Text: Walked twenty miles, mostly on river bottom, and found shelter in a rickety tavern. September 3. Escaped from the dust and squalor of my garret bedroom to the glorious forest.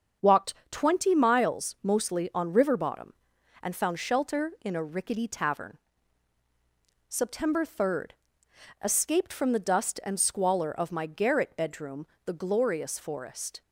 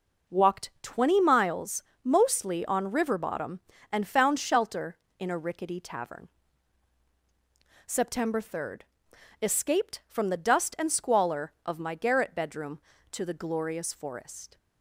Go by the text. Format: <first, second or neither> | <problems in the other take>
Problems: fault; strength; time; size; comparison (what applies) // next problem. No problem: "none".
second | starts louder than the rest; until 1.4 s; 7 dB // pauses between "Walked" and "twenty"; slight; at 0.5 s; 0.18 s long // skips "to"; at 12.1 s